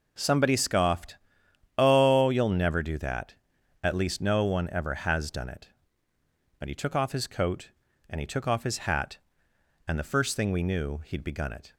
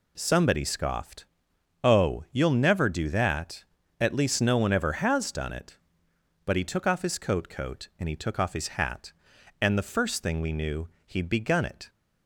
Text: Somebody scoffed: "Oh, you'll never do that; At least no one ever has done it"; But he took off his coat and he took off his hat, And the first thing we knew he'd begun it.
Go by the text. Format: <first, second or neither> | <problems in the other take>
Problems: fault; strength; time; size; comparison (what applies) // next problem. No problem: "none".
first | says "coat" twice; at 7.4 s // pauses between "knew" and "he'd"; slight; at 10.8 s; 0.18 s long